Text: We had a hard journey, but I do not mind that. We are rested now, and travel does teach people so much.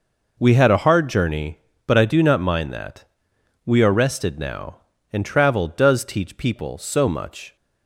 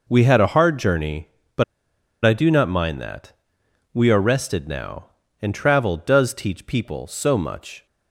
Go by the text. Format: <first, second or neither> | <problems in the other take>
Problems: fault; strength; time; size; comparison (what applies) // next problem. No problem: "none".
first | pauses between "but" and "I"; noticeable; at 1.6 s; 0.61 s long